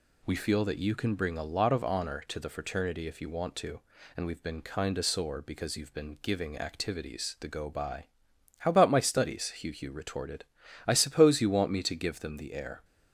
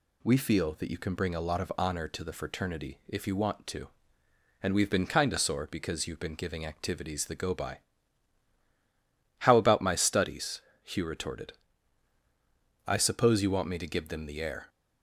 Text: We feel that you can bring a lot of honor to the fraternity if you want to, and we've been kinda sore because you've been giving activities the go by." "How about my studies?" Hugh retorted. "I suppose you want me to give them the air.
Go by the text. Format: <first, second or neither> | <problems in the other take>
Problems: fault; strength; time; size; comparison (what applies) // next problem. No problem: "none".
second | says "Hugh" twice; at 9.7 s